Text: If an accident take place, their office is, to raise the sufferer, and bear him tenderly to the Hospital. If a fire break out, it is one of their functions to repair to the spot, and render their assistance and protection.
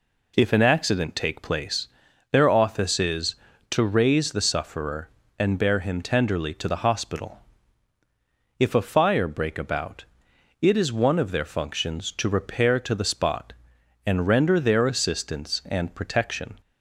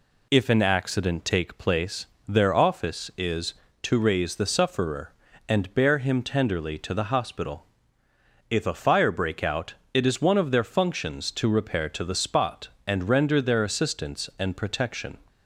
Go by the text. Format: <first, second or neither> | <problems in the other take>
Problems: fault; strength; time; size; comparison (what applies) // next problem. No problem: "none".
second | says "about" for "out"; at 9.5 s